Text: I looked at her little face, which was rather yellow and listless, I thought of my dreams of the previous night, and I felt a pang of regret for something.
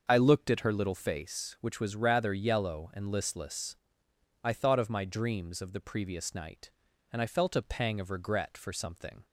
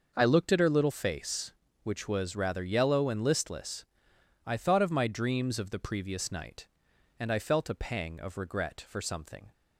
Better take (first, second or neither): neither